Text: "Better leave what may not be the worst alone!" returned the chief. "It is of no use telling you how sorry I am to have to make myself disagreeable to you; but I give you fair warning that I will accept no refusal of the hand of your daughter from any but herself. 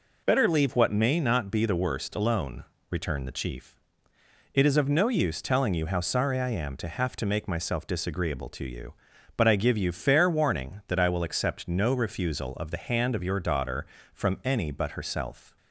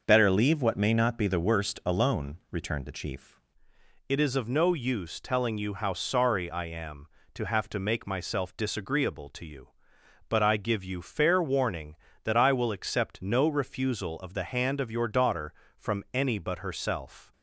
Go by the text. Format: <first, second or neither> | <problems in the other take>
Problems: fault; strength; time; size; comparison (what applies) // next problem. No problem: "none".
first | changes voice at "It"; from 4.0 s on; 13.3 s long